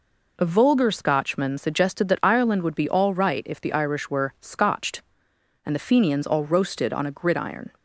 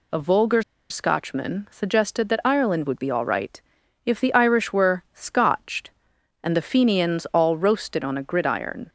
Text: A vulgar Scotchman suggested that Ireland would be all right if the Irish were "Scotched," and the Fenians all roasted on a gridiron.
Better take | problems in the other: first | pauses between "vulgar" and "Scotchman"; slight; at 0.6 s; 0.27 s long // pauses between "right" and "if"; at 3.6 s; 0.44 s long

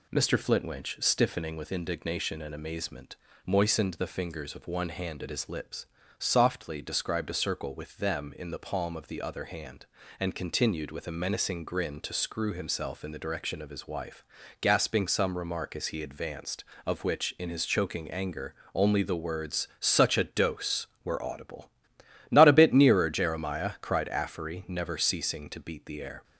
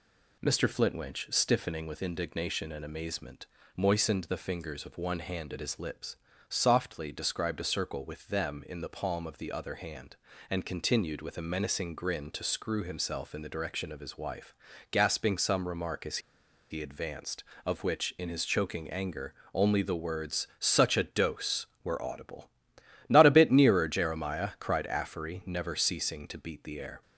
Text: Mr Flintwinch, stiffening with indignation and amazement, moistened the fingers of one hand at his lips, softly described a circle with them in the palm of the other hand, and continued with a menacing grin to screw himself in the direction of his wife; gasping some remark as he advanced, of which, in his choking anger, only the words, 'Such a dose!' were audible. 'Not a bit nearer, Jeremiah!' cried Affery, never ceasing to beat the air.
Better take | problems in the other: first | pauses between "as" and "he"; noticeable; at 16.1 s; 0.52 s long

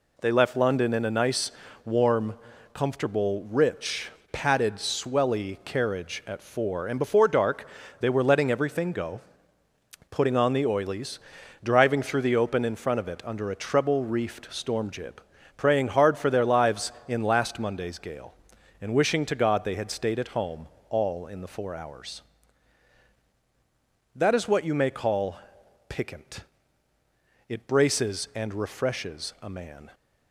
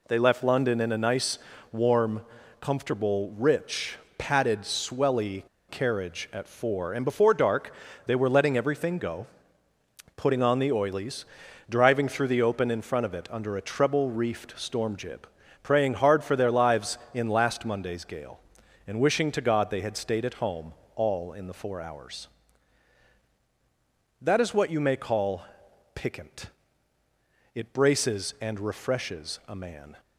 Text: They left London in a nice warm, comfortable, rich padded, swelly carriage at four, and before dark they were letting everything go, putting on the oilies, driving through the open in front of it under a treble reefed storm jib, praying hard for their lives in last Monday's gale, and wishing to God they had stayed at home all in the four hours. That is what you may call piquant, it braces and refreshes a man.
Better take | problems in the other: first | pauses between "nice" and "warm"; slight; at 1.3 s; 0.34 s long; slight in the first // pauses between "rich" and "padded"; slight; at 3.9 s; 0.20 s long; slight in the first // pauses between "swelly" and "carriage"; slight; at 5.4 s; 0.26 s long // pauses between "dark" and "they"; slight; at 7.7 s; 0.34 s long; slight in the first // pauses between "home" and "all"; slight; at 20.7 s; 0.20 s long; slight in the first // pauses between "call" and "piquant"; noticeable; at 25.4 s; 0.50 s long; noticeable in the first

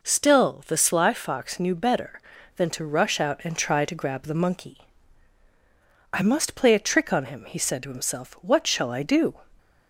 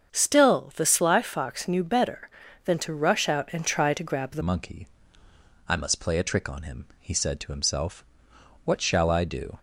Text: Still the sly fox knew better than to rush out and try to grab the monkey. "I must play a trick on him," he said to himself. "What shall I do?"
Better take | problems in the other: first | starts louder than the rest; strong; until 1.1 s; 7.5 dB // changes voice at "monkey"; from 4.4 s on; 5.1 s long

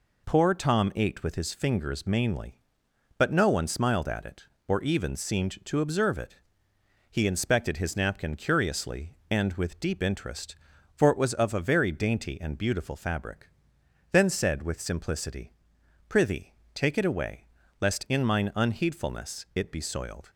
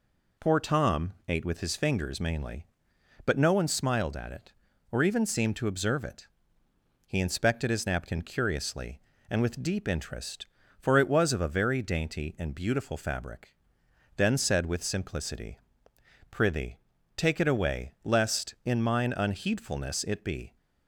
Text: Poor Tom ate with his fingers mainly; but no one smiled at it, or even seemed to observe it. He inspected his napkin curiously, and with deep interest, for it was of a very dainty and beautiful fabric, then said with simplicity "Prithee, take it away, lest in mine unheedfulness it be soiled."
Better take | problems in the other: first | pauses between "simplicity" and "Prithee"; noticeable; at 15.5 s; 0.74 s long; noticeable in the first // stops before "soiled"; at 20.5 s

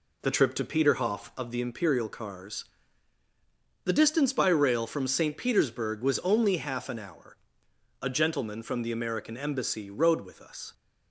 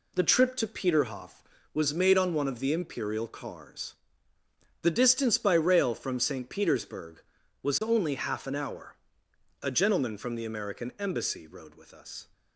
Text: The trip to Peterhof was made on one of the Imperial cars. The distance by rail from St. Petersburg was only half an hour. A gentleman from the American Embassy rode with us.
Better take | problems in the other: second | skips "was made on one"; at 1.3 s

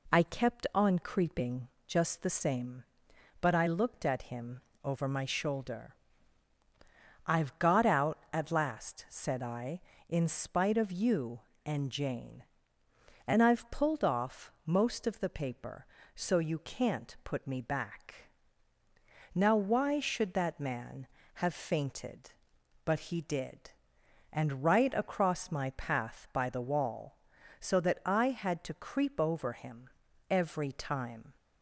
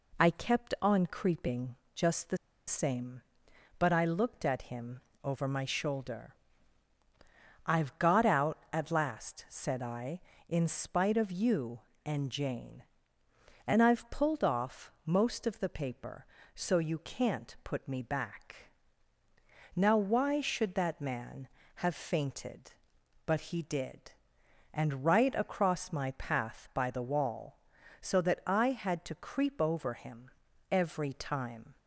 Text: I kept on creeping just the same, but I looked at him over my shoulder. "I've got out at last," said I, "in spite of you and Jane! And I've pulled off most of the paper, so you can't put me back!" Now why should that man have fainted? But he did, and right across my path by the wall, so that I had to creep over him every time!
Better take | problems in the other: first | pauses between "creeping" and "just"; slight; at 1.7 s; 0.22 s long; slight in the first // pauses between "the" and "same"; slight; at 2.3 s; 0.31 s long // pauses between "him" and "over"; slight; at 5.0 s; 0.22 s long; slight in the first // pauses between "him" and "every"; at 30.3 s; 0.40 s long; also in the first

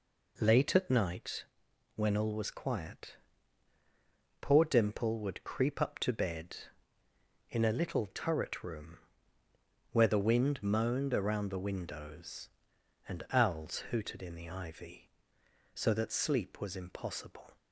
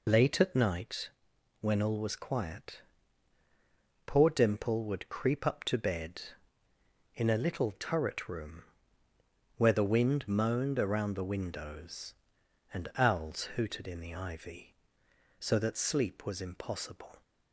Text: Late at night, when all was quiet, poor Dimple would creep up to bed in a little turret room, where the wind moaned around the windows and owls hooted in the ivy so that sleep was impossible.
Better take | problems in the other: first | loses the start of "Late"; at 0.0 s; 40 ms

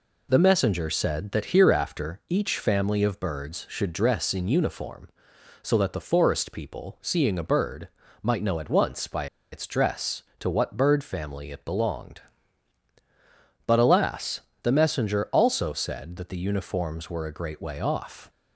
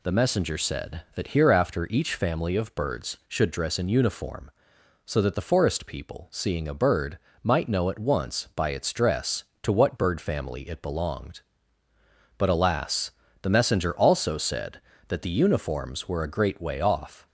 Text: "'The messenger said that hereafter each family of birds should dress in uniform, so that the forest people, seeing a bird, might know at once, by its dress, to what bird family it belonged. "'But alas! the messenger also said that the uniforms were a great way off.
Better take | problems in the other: second | pauses between "by" and "its"; slight; at 9.2 s; 0.28 s long

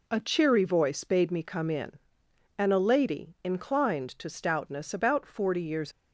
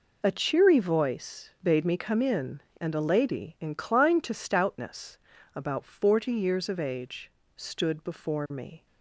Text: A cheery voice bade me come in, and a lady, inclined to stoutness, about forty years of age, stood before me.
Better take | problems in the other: second | stops before "of age stood before me"; at 5.9 s

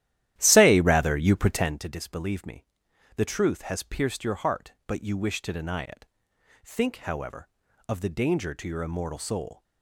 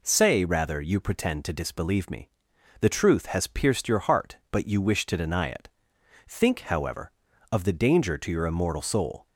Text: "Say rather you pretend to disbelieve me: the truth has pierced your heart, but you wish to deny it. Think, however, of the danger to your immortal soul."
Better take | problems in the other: second | starts louder than the rest; strong; until 1.8 s; 13 dB

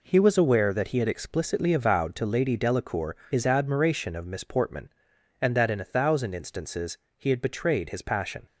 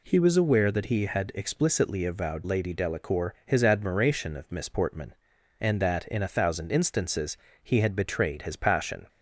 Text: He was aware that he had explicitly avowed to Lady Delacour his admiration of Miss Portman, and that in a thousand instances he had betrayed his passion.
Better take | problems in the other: first | skips "to"; at 2.4 s // pauses between "instances" and "he"; slight; at 7.3 s; 0.26 s long; slight in the first

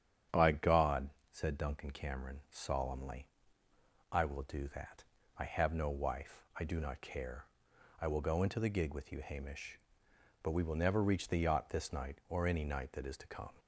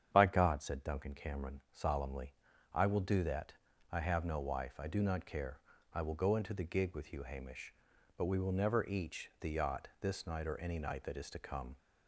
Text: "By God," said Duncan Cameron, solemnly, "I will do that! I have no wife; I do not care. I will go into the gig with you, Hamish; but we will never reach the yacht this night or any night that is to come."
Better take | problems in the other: first | starts louder than the rest; strong; until 1.1 s; 8.5 dB; strong in the first // says "each" for "reach"; at 8.8 s

